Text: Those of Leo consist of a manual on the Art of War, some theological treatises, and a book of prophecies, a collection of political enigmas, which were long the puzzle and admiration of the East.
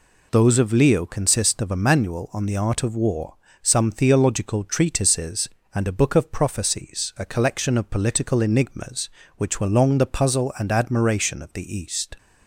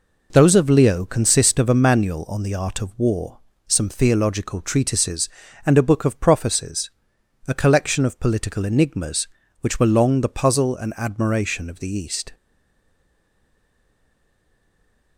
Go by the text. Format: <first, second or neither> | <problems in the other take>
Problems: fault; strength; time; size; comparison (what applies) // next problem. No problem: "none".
first | stays silent after the last word; strong; from 12.3 s on; 2.8 s long